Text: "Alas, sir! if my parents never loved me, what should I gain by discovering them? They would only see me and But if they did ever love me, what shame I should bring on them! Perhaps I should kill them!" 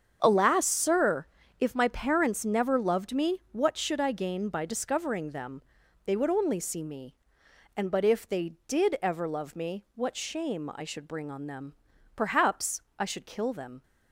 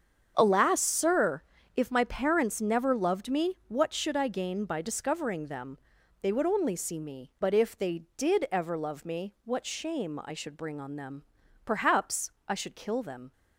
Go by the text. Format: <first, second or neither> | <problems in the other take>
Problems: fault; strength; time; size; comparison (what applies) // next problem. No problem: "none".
first | starts louder than the rest; strong; until 1.3 s; 7.5 dB; strong in the first // skips "and"; at 7.3 s // pauses between "Perhaps" and "I"; slight; at 12.2 s; 0.18 s long; slight in the first